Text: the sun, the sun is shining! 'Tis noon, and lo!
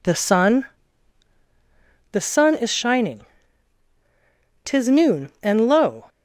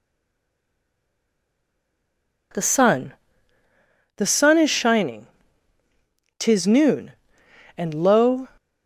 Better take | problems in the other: first | stays silent before the first word; until 2.5 s; 2.5 s long

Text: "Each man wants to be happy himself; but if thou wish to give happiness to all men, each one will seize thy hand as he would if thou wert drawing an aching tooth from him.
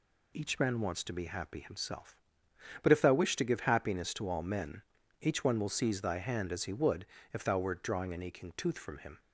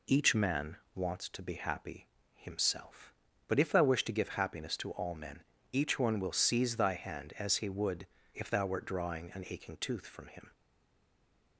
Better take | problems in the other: first | pauses between "man" and "wants"; slight; at 0.7 s; 0.18 s long // pauses between "happy" and "himself"; slight; at 2.0 s; 0.26 s long // pauses between "would" and "if"; slight; at 8.0 s; 0.26 s long; slight in the first // stays silent after the last word; from 10.5 s on; 1.0 s long

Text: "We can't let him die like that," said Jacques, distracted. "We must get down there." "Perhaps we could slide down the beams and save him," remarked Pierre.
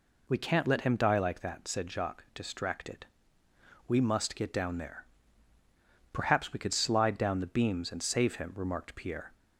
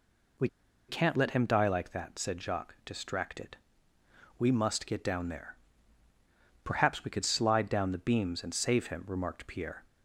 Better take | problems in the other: first | pauses between "We" and "can't"; at 0.4 s; 0.41 s long

